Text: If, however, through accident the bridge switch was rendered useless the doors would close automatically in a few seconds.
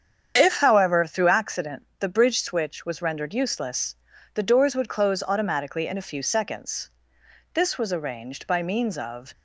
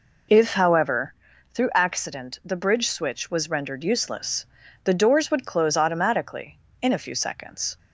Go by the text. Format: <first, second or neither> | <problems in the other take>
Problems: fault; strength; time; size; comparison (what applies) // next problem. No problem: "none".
second | starts louder than the rest; strong; until 1.3 s; 8 dB // pauses between "useless" and "the"; at 3.9 s; 0.40 s long; also in the second // goes on to say "This was arranged by means of"; strong; from 7.5 s on; 1.7 s long